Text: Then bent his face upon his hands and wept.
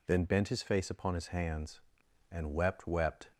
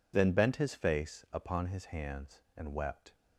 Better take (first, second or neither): second